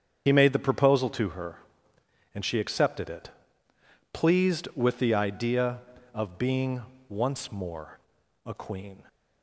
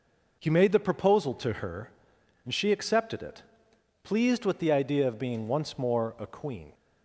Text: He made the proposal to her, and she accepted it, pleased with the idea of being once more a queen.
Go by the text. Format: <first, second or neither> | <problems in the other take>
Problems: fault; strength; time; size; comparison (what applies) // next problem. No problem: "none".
second | loses the start of "He"; at 0.2 s; 65 ms // starts louder than the rest; strong; until 1.2 s; 8 dB // pauses between "being" and "once"; slight; at 6.8 s; 0.26 s long // pauses between "more" and "a"; noticeable; at 7.9 s; 0.46 s long